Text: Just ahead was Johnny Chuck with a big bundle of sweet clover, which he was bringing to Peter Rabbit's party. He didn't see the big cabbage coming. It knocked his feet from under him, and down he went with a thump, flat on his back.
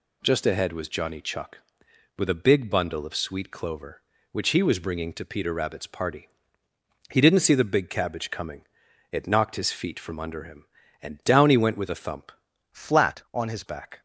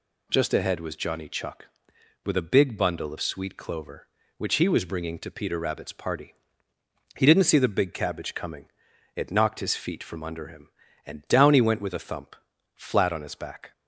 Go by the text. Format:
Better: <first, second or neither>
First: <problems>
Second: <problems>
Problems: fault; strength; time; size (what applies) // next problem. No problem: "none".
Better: second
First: changes voice from "flat" to "his"; from 12.7 to 13.6 s; 0.9 s long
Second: none